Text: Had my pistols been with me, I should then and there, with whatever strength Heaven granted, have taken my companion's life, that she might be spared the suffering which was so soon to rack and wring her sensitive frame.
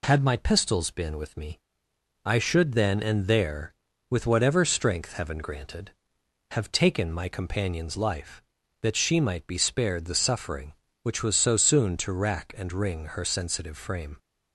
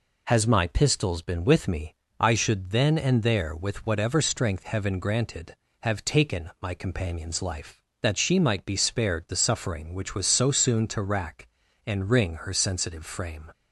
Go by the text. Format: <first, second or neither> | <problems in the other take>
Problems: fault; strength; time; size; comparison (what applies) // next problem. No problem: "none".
first | says "Has" for "Had"; at 0.2 s